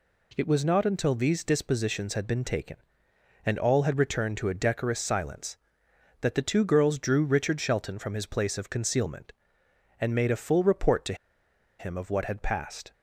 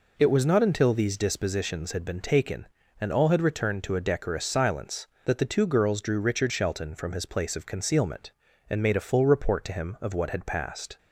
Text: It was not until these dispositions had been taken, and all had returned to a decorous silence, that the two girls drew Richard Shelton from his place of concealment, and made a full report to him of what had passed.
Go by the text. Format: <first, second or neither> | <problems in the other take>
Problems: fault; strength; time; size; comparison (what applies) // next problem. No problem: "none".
second | pauses between "to" and "him"; noticeable; at 11.1 s; 0.65 s long